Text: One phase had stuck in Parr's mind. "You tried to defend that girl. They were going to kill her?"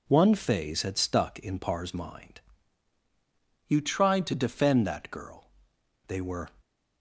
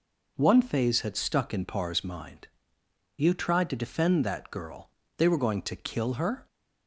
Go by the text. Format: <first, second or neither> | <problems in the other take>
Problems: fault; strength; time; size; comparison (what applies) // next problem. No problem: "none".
second | stops before "going to kill her"; at 6.6 s